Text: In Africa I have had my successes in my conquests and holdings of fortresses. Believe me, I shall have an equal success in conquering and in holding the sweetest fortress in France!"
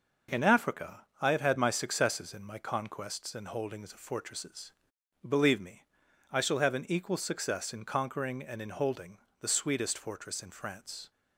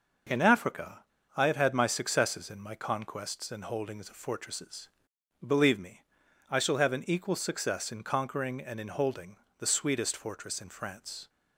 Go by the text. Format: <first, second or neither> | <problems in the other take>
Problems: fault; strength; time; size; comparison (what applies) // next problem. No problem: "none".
first | pauses between "Africa" and "I"; slight; at 1.0 s; 0.31 s long // pauses between "holding" and "the"; slight; at 9.3 s; 0.22 s long; slight in the first